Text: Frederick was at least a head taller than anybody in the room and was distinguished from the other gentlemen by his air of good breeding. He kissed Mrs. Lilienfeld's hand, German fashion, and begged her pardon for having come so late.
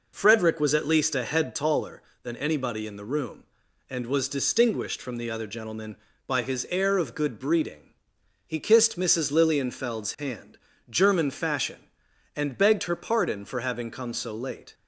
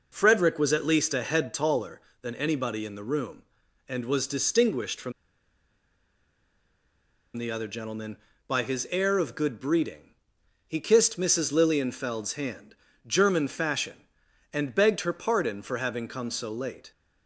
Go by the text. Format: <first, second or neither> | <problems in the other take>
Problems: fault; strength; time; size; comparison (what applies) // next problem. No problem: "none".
first | pauses between "from" and "the"; strong; at 5.1 s; 2.2 s long